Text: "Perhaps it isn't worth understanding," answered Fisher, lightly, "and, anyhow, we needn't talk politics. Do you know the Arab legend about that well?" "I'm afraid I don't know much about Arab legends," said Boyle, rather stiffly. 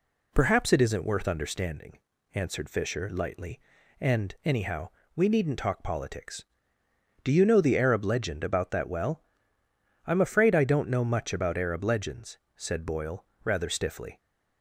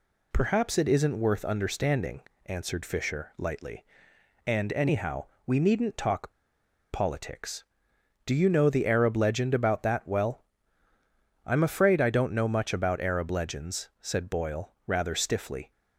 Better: first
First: none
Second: pauses between "talk" and "politics"; noticeable; at 6.3 s; 0.61 s long

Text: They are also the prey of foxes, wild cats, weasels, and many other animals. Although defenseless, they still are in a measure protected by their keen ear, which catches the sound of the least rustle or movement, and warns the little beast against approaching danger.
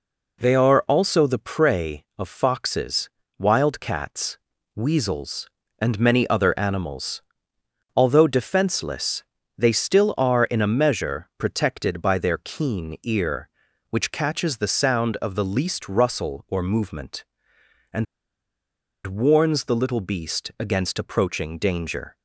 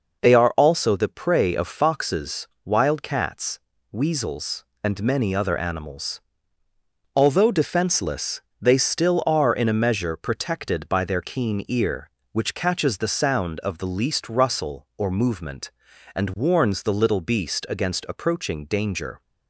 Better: second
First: pauses between "and" and "warns"; at 18.0 s; 1.0 s long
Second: none

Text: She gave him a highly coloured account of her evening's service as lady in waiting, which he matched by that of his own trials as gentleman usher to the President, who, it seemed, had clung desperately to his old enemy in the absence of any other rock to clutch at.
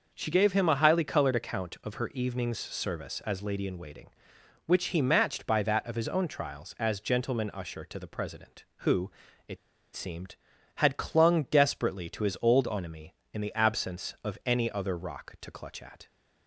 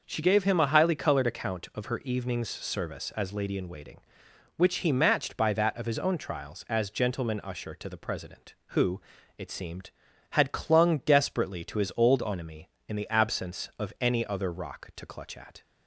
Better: second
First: pauses between "it" and "seemed"; at 9.5 s; 0.37 s long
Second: none

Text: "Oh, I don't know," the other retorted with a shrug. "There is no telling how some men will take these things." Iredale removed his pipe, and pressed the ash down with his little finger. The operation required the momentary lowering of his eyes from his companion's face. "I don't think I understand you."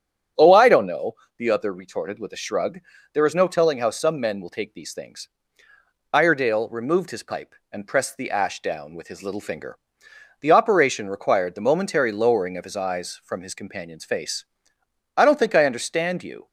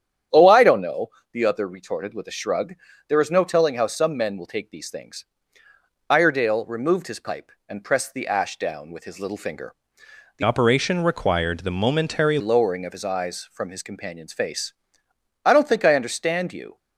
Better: first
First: starts louder than the rest; strong; until 1.6 s; 8 dB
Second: starts louder than the rest; strong; until 1.5 s; 9.5 dB // changes voice from "operation" to "momentary"; from 10.4 to 12.3 s; 1.9 s long

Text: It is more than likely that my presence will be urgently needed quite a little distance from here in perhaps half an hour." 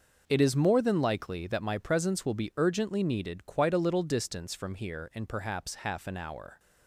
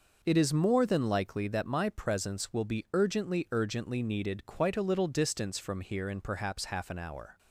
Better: first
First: none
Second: says "urgently" twice; at 3.4 s

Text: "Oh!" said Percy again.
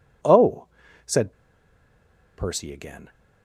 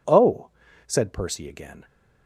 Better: second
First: pauses between "said" and "Percy"; at 1.3 s; 1.0 s long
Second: none

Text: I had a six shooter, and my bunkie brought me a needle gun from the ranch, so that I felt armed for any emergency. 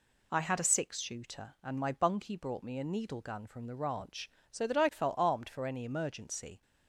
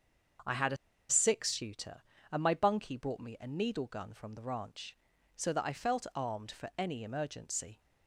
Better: first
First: none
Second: starts louder than the rest; until 1.8 s; 6.5 dB // pauses between "a" and "six"; slight; at 0.7 s; 0.32 s long

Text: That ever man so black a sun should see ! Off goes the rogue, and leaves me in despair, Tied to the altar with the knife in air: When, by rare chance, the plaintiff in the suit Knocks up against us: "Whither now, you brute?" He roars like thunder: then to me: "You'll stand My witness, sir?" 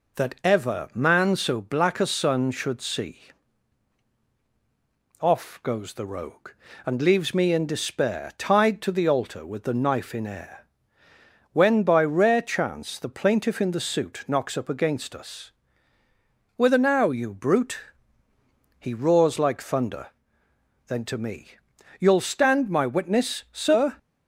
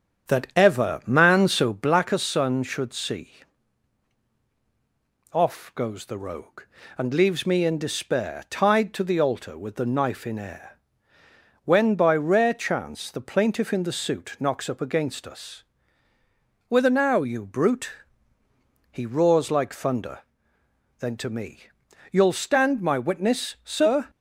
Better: first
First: none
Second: starts louder than the rest; strong; until 2.2 s; 8 dB

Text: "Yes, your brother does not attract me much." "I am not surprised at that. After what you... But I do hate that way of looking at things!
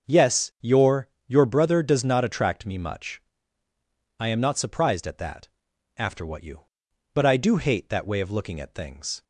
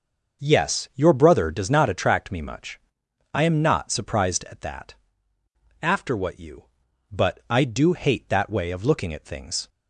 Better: second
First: starts louder than the rest; noticeable; until 1.3 s; 6 dB // says "your" twice; at 1.2 s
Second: starts louder than the rest; until 1.4 s; 6 dB

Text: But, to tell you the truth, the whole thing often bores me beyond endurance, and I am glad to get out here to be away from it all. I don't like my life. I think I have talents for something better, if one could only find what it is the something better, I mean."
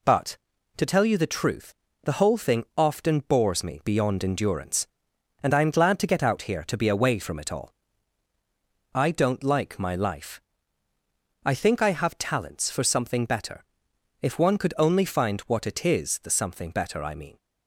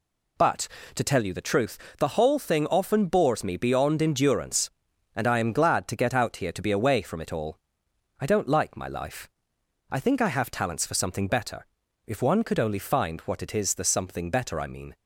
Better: neither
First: none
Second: none

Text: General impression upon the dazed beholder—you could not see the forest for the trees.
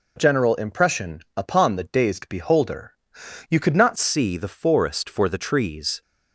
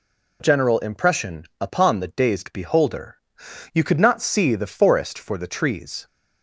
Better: second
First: pauses between "impression" and "upon"; slight; at 1.2 s; 0.16 s long // changes voice at "see"; from 3.9 s on; 2.1 s long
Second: pauses between "impression" and "upon"; slight; at 1.4 s; 0.16 s long

